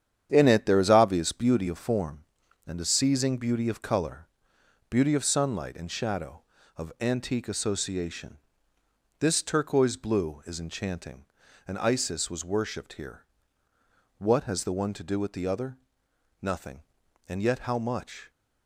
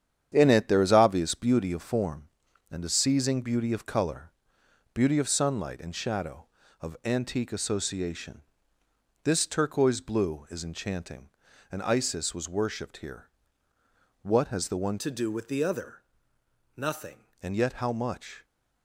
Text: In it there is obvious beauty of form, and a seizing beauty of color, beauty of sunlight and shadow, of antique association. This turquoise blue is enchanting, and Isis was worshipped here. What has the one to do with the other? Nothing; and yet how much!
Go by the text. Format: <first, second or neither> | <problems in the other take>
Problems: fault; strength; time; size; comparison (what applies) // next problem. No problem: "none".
first | starts louder than the rest; strong; until 1.3 s; 9 dB; strong in the first // changes voice from "to" to "Nothing"; from 14.9 to 17.1 s; 2.2 s long